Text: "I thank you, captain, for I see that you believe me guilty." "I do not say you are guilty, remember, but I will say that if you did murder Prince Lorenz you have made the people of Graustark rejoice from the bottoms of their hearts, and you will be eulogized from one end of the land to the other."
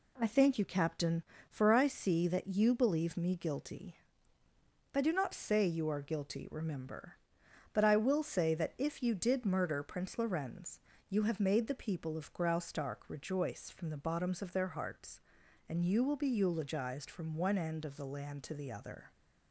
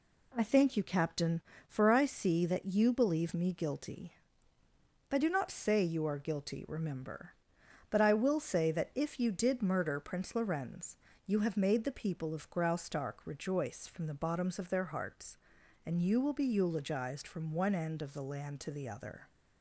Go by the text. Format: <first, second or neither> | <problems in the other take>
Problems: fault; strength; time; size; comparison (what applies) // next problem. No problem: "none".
neither | pauses between "Lorenz" and "you"; slight; the same in both